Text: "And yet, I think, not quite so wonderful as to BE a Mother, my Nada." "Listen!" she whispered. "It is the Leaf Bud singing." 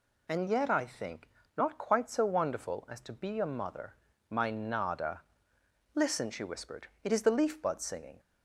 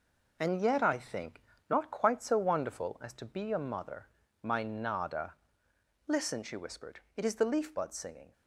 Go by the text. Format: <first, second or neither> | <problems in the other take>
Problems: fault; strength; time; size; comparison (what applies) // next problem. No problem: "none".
first | gets quieter; throughout; 6.5 dB